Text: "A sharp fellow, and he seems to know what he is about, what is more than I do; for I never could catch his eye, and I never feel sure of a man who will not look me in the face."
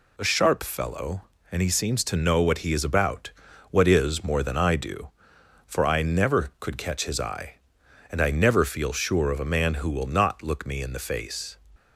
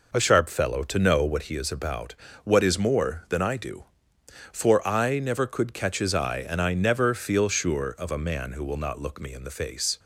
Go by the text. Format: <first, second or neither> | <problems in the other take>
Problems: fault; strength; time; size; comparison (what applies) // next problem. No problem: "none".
first | skips "and he seems"; at 0.8 s